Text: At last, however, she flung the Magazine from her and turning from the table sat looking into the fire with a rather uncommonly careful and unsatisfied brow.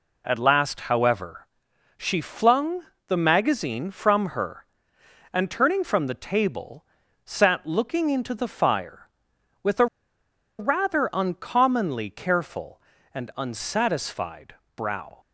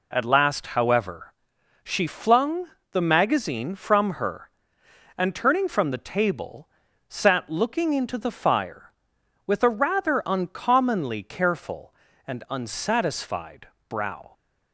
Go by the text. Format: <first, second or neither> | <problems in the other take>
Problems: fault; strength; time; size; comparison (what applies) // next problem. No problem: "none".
second | pauses between "flung" and "the"; slight; at 2.8 s; 0.24 s long; slight in the second // pauses between "table" and "sat"; at 6.8 s; 0.42 s long; also in the second // pauses between "a" and "rather"; noticeable; at 9.8 s; 0.73 s long // pauses between "unsatisfied" and "brow"; slight; at 14.5 s; 0.20 s long; slight in the second